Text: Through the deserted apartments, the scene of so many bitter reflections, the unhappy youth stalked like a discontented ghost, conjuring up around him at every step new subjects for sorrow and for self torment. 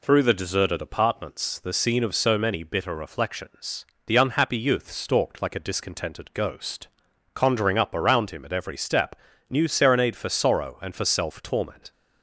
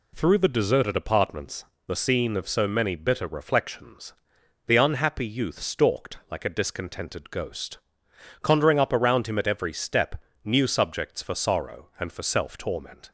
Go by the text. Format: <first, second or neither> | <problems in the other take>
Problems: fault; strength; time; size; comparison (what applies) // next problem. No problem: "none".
second | pauses between "step" and "new"; slight; at 9.1 s; 0.32 s long; slight in the second // says "serenade" for "subjects"; at 9.6 s